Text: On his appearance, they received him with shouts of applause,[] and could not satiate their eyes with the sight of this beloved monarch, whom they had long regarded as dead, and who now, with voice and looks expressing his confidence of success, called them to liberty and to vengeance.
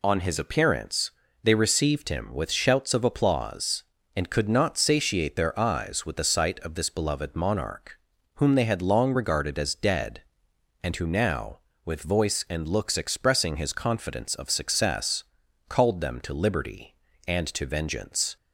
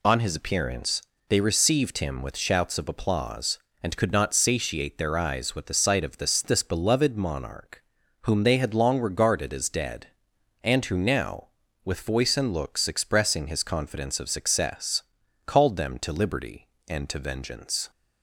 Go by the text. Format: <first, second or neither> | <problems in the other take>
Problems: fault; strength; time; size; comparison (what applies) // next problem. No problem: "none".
first | says "this" twice; at 6.4 s